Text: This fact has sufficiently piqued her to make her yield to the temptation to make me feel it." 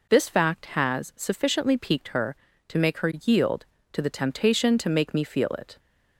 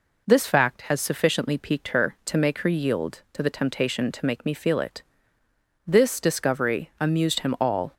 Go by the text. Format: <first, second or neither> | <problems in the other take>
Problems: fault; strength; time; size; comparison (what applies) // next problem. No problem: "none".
first | goes on to say "This discovery amused him all"; strong; from 5.8 s on; 2.0 s long